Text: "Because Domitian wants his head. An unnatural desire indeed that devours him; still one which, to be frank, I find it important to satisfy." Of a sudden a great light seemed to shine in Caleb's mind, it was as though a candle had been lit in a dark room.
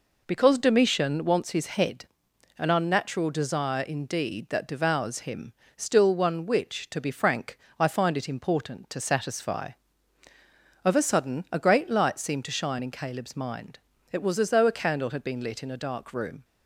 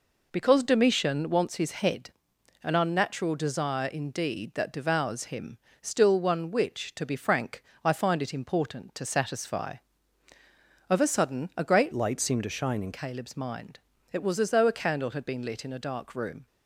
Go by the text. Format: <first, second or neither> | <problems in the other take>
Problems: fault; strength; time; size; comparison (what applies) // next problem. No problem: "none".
first | changes voice from "light" to "in"; from 11.9 to 12.9 s; 1.0 s long